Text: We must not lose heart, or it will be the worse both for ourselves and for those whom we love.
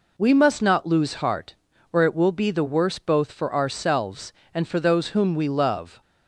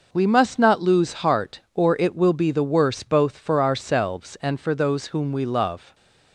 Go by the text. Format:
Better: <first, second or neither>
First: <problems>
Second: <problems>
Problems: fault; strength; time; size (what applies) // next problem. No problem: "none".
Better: neither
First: none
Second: none